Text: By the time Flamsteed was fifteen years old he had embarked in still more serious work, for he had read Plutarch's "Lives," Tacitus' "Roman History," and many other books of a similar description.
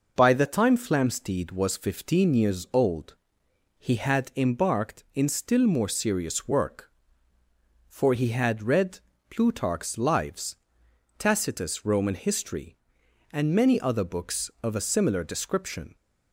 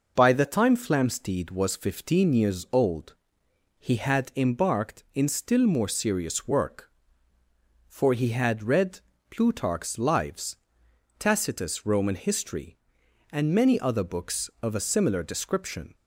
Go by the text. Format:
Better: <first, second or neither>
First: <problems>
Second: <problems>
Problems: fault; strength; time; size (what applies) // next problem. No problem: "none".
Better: neither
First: pauses between "old" and "he"; noticeable; at 3.1 s; 0.64 s long // pauses between "read" and "Plutarch's"; slight; at 8.9 s; 0.30 s long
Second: pauses between "old" and "he"; noticeable; at 3.1 s; 0.66 s long // pauses between "read" and "Plutarch's"; slight; at 8.9 s; 0.30 s long